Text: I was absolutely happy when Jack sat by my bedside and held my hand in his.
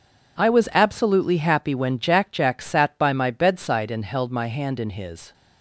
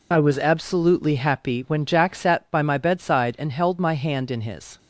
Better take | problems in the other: second | says "Jack" twice; at 2.3 s

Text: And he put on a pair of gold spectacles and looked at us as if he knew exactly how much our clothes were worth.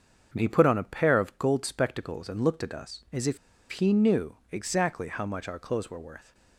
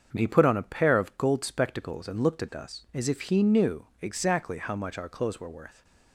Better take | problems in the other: second | starts louder than the rest; until 1.3 s; 7 dB; also in the second // pauses between "if" and "he"; slight; at 3.3 s; 0.34 s long

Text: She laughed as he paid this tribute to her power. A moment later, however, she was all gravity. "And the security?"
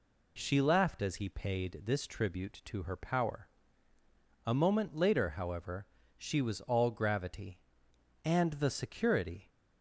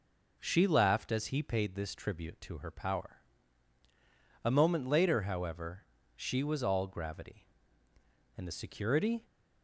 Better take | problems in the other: neither | none

